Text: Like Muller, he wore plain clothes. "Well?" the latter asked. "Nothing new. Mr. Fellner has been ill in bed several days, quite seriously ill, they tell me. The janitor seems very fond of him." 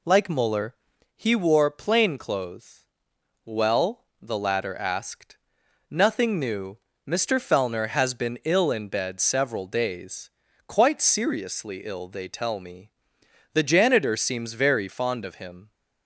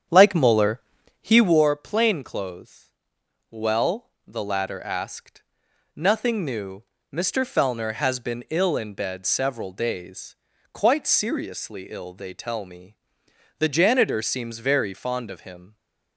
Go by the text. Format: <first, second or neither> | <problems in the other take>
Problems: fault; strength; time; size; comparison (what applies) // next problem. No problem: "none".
first | starts louder than the rest; strong; until 1.6 s; 8.5 dB